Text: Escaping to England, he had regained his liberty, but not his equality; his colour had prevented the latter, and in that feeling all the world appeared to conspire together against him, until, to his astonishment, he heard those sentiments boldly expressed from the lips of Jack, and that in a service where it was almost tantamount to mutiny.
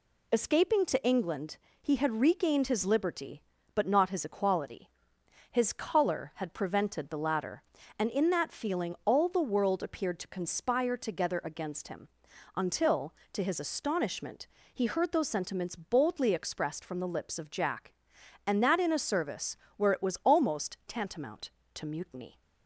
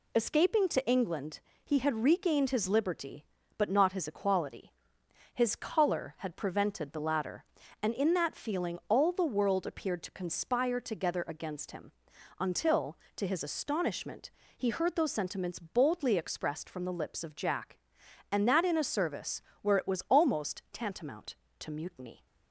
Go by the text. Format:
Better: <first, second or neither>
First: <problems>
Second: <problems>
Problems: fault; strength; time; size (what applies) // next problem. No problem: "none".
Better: neither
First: pauses between "service" and "where"; slight; at 19.5 s; 0.20 s long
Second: pauses between "service" and "where"; slight; at 19.4 s; 0.20 s long